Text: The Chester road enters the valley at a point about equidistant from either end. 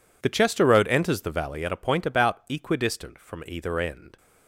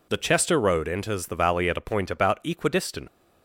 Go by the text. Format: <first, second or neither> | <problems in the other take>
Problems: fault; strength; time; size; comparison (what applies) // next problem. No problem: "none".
first | stops before "from either end"; at 3.0 s